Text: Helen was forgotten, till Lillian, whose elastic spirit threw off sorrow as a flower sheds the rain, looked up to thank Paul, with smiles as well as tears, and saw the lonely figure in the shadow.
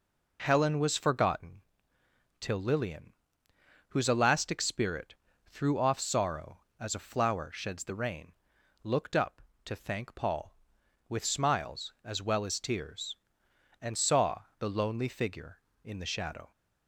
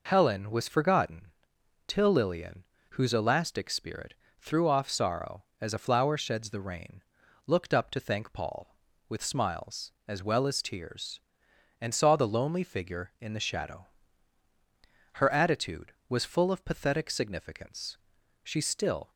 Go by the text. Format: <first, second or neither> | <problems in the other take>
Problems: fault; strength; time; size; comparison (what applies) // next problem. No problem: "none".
first | pauses between "spirit" and "threw"; slight; at 4.1 s; 0.24 s long; slight in the first // goes on to say "Her attitude was full of pathetic significance she still"; strong; from 15.1 s on; 3.9 s long